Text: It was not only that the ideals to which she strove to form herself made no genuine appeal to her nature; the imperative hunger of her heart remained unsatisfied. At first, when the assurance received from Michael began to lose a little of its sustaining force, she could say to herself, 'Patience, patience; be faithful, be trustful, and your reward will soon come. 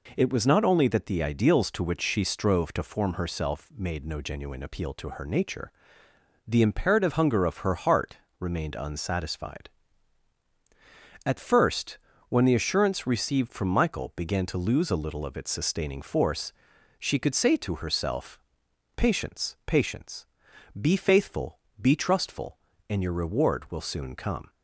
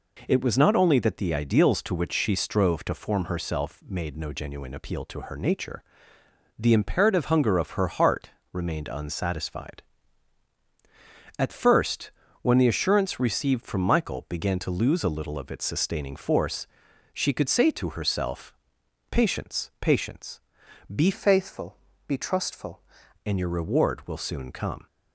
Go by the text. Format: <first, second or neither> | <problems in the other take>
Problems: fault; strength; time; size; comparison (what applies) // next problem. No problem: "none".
first | pauses between "heart" and "remained"; slight; at 8.2 s; 0.22 s long; slight in the first // changes voice from "faithful" to "trustful"; from 21.1 to 22.7 s; 1.6 s long